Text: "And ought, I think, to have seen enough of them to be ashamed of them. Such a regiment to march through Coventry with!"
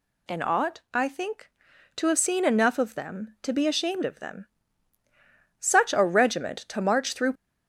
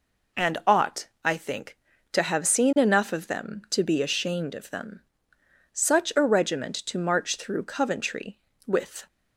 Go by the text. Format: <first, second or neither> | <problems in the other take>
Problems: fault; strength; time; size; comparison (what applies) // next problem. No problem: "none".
second | stops before "Coventry with"; at 7.3 s